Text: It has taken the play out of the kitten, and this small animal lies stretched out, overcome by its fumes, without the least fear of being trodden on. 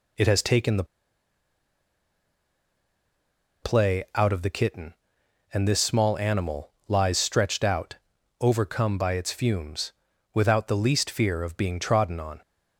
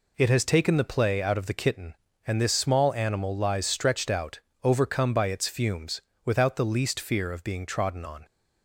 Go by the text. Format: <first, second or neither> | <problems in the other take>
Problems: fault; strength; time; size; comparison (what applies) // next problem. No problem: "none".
second | pauses between "the" and "play"; strong; at 0.8 s; 2.7 s long // pauses between "animal" and "lies"; slight; at 6.7 s; 0.16 s long